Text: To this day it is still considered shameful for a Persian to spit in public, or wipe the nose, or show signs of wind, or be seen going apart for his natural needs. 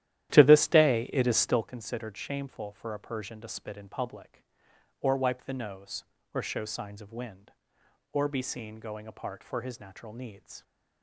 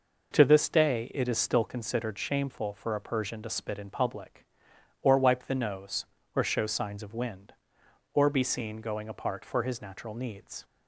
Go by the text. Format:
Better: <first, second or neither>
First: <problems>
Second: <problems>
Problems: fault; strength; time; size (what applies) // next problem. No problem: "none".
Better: second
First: starts louder than the rest; strong; until 1.7 s; 12.5 dB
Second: none